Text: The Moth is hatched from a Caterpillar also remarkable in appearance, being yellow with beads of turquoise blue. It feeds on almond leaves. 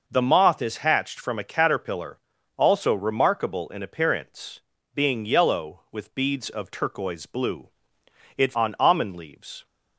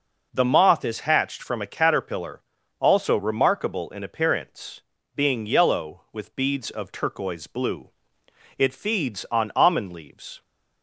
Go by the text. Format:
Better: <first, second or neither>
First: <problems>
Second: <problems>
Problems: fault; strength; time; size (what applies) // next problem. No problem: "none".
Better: second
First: pauses between "Caterpillar" and "also"; slight; at 2.1 s; 0.36 s long // skips "feeds"; at 8.5 s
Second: pauses between "Caterpillar" and "also"; slight; at 2.4 s; 0.36 s long